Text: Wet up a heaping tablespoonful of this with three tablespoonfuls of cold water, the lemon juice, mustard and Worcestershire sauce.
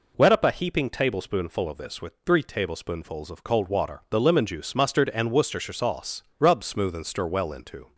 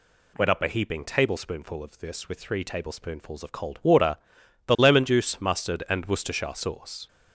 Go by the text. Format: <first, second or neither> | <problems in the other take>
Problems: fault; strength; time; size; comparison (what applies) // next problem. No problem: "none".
second | goes on to say "Rub smooth and stir well into"; from 6.3 s on; 1.5 s long